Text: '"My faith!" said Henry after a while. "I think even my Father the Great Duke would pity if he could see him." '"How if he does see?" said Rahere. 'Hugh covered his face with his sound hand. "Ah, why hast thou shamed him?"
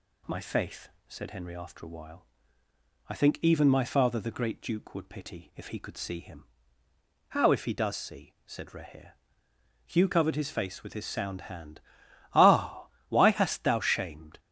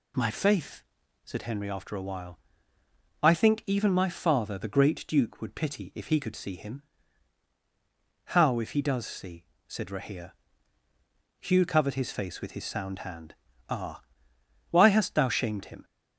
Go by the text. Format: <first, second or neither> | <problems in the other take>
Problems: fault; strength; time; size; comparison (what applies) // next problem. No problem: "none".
second | stops before "him"; at 14.3 s